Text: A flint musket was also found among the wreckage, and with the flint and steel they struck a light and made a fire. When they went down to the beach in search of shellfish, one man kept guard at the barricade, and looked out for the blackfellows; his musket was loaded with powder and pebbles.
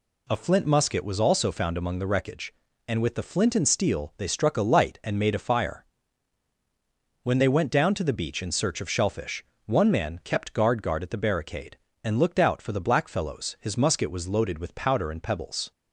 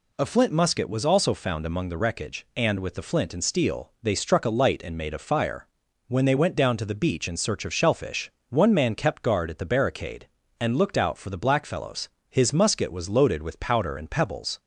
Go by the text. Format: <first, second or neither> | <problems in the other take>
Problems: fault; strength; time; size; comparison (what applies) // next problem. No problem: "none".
second | says "guard" twice; at 10.8 s